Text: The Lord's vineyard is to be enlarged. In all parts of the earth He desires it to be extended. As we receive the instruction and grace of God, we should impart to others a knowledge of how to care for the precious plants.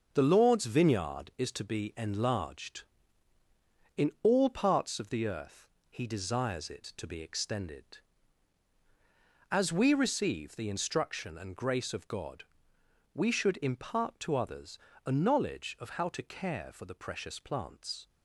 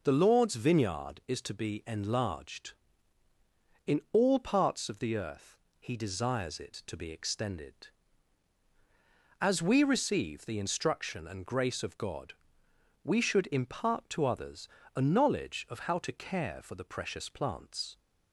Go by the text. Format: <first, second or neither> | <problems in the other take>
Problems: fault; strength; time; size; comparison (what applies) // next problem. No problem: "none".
second | gets quieter; throughout; 7 dB // pauses between "earth" and "He"; slight; at 5.6 s; 0.20 s long; slight in the second // pauses between "others" and "a"; slight; at 14.7 s; 0.28 s long; slight in the second